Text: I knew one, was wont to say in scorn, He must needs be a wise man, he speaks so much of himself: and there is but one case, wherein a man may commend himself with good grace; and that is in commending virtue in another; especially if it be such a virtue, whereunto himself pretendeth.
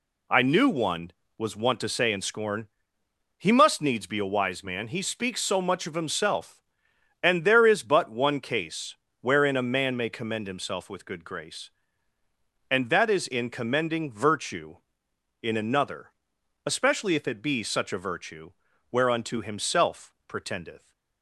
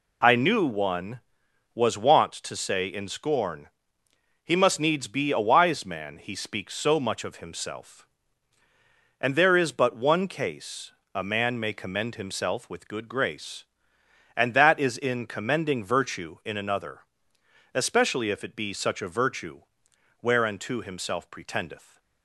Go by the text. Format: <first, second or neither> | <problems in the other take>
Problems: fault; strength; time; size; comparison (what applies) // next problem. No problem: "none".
first | skips "wherein"; at 11.0 s